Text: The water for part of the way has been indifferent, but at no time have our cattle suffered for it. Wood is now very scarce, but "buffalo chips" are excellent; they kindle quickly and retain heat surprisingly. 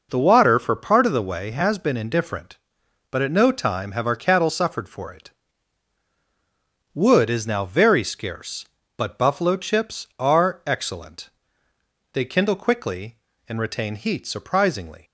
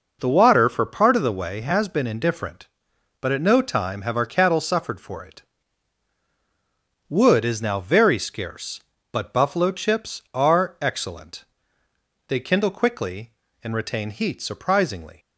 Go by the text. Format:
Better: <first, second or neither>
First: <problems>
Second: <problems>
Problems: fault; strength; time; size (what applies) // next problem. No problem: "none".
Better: neither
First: none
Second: none